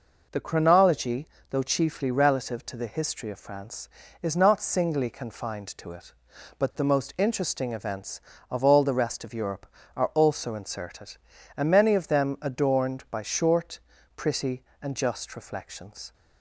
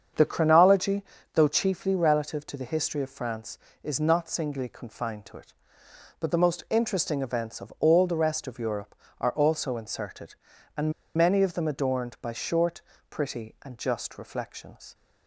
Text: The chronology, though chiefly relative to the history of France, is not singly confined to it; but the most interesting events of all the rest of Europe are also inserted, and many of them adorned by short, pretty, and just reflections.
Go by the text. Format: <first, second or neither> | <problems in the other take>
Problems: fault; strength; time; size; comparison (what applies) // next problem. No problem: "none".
first | starts louder than the rest; strong; until 1.4 s; 7.5 dB // pauses between "and" and "many"; slight; at 10.9 s; 0.23 s long